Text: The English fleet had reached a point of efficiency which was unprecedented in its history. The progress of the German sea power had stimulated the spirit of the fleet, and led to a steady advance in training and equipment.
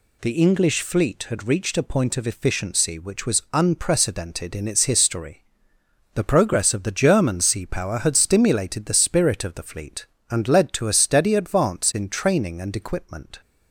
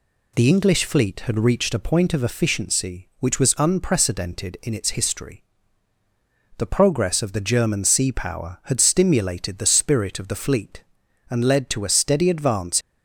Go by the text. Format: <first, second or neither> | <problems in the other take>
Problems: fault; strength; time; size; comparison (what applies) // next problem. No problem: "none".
first | stops before "in training and equipment"; at 12.8 s